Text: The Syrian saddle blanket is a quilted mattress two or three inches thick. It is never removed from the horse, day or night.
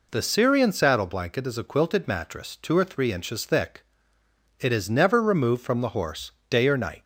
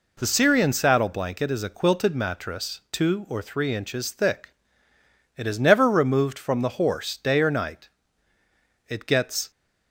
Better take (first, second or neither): first